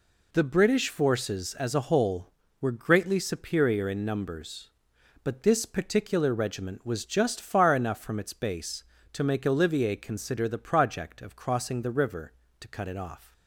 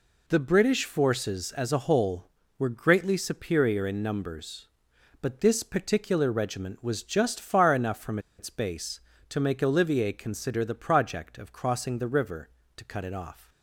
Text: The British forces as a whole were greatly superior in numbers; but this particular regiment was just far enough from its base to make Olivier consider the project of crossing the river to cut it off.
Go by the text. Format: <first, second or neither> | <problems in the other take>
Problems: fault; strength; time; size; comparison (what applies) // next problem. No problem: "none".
first | pauses between "from" and "its"; slight; at 8.1 s; 0.20 s long